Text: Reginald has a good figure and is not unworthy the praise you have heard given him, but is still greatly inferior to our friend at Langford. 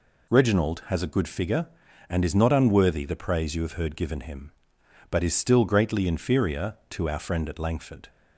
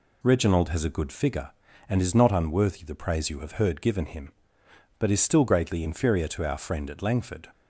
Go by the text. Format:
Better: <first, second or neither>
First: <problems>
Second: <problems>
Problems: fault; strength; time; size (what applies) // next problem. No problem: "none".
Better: neither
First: none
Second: none